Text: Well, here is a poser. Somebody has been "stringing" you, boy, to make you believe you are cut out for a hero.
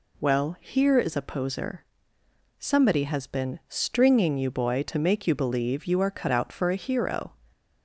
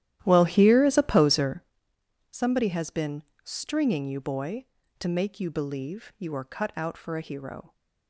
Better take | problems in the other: first | starts louder than the rest; strong; until 1.7 s; 12.5 dB // pauses between "been" and "stringing"; slight; at 3.2 s; 0.20 s long

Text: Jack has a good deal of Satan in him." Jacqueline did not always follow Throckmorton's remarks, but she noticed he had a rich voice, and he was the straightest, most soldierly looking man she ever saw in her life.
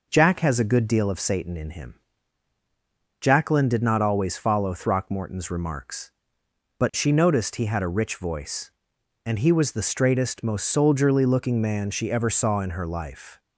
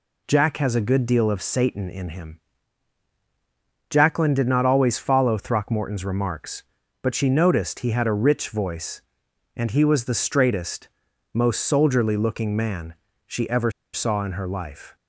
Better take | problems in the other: first | pauses between "man" and "she"; slight; at 12.9 s; 0.32 s long // pauses between "ever" and "saw"; slight; at 13.6 s; 0.23 s long

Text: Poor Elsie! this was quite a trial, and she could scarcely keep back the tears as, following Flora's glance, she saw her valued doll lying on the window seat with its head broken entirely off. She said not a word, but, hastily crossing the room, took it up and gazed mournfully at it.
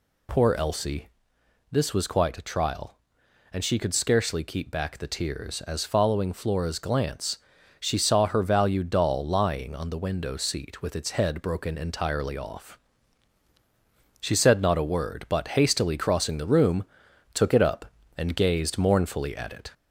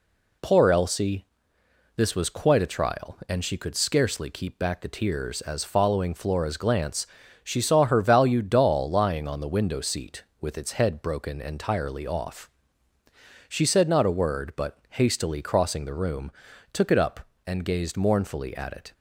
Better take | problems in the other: second | gets louder; slight; throughout; 2.5 dB

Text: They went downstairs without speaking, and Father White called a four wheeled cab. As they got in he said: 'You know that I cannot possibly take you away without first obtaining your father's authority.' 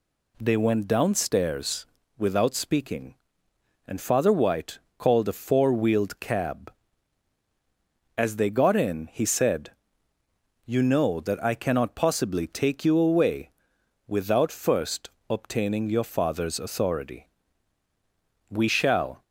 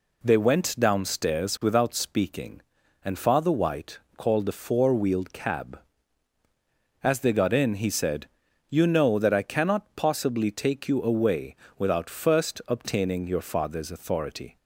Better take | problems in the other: second | pauses between "downstairs" and "without"; slight; at 1.8 s; 0.32 s long // pauses between "White" and "called"; slight; at 4.7 s; 0.18 s long; slight in the second // pauses between "away" and "without"; noticeable; at 13.4 s; 0.58 s long; slight in the second // pauses between "first" and "obtaining"; slight; at 15.0 s; 0.18 s long // goes on to say "We shall"; noticeable; from 18.4 s on; 0.74 s long

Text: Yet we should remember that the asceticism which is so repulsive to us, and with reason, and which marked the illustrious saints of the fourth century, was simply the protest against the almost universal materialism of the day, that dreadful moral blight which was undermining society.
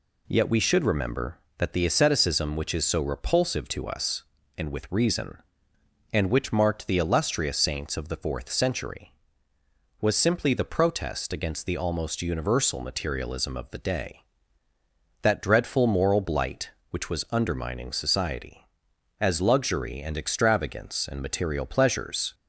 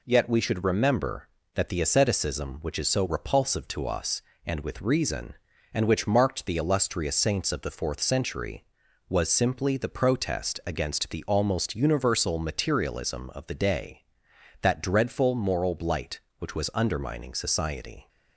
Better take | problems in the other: second | goes on to say "As luxury and extravagance and material pleasures"; strong; from 19.1 s on; 3.1 s long

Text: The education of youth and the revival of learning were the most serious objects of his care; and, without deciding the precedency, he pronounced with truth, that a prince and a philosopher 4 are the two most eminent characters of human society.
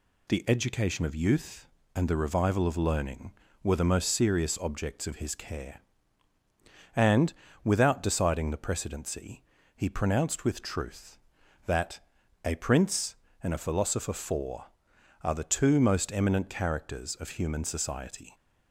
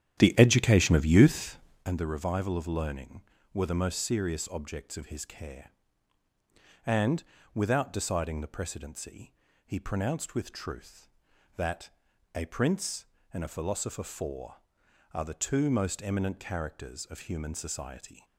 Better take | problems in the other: first | starts louder than the rest; strong; until 1.9 s; 10.5 dB // pauses between "that" and "a"; at 11.9 s; 0.44 s long; also in the first

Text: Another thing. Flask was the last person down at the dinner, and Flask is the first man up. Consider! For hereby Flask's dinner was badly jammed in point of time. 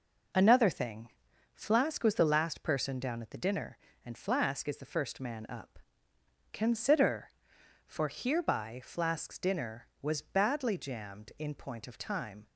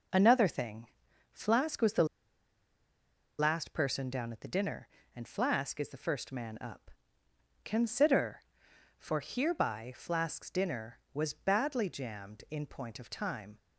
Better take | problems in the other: first | pauses between "the" and "last"; strong; at 2.0 s; 1.3 s long

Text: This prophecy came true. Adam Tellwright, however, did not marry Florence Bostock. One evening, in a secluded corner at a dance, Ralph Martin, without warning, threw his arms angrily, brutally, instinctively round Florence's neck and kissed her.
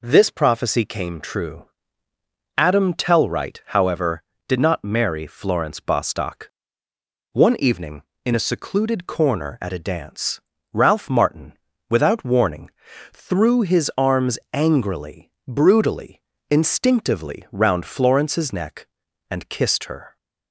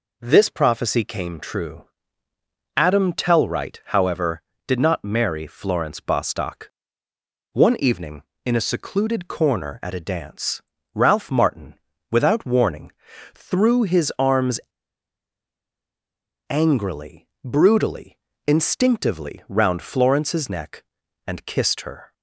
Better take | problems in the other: first | pauses between "arms" and "angrily"; strong; at 14.5 s; 1.8 s long

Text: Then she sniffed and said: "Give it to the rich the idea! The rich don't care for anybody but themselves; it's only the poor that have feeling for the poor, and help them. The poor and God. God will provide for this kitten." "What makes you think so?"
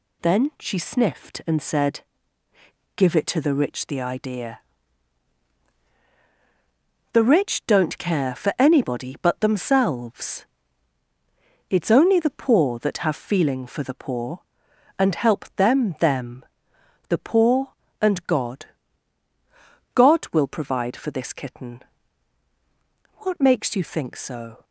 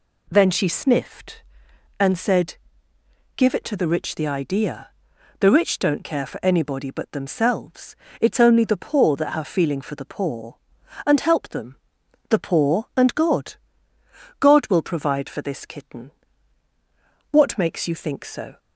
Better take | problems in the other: second | says "them" twice; at 16.0 s

